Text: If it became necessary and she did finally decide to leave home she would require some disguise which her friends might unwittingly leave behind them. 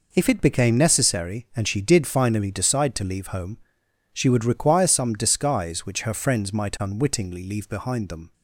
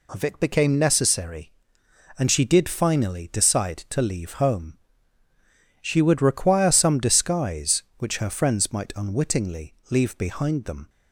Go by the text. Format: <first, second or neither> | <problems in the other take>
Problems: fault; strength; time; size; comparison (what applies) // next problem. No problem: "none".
first | says "Of" for "If"; at 0.1 s // pauses between "home" and "she"; at 4.7 s; 1.0 s long; noticeable in the first